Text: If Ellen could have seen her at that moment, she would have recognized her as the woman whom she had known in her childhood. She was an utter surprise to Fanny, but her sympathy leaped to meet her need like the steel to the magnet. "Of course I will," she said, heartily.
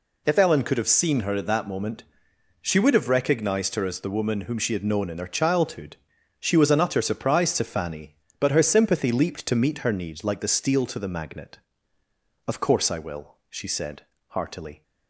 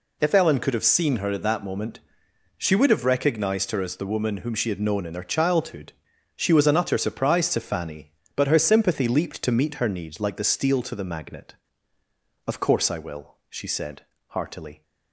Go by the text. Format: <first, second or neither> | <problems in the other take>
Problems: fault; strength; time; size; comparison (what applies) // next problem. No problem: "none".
neither | none